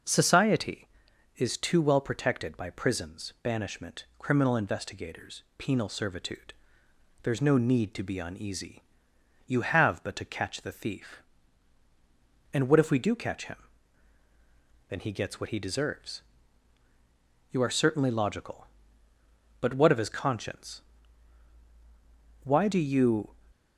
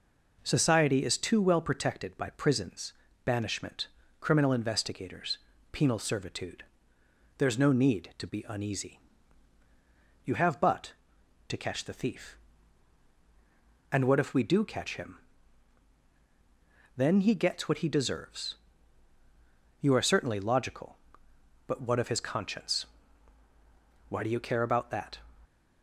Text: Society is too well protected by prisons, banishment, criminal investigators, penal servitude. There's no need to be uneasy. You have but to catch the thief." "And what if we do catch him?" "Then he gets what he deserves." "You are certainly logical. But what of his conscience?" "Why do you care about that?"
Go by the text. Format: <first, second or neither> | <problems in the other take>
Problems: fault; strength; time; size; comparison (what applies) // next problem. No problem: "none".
second | stops before "care about that"; at 23.5 s